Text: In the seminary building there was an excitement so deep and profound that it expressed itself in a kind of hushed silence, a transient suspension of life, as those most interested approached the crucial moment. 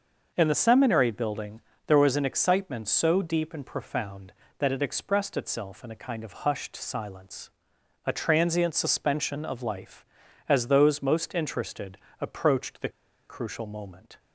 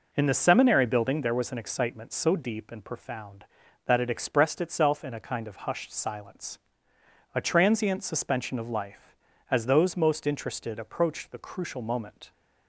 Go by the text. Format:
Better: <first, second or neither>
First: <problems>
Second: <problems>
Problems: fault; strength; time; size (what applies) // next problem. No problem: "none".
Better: second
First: pauses between "building" and "there"; slight; at 1.6 s; 0.26 s long // pauses between "interested" and "approached"; slight; at 11.9 s; 0.20 s long // pauses between "the" and "crucial"; at 12.8 s; 0.41 s long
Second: none